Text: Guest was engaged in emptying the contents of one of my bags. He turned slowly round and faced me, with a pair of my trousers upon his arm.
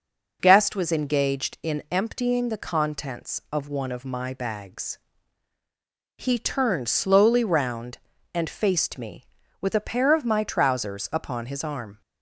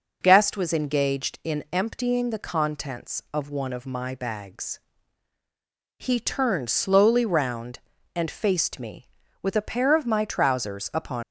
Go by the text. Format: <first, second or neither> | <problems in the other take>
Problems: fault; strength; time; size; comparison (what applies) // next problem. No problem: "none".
first | stops before "his arm"; at 11.2 s